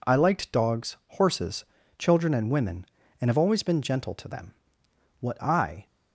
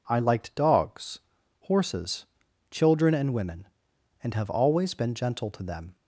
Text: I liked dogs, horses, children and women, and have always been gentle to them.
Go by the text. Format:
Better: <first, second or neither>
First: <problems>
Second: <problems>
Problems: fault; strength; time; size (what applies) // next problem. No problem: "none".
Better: second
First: goes on to say "What I"; noticeable; from 5.2 s on; 0.64 s long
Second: none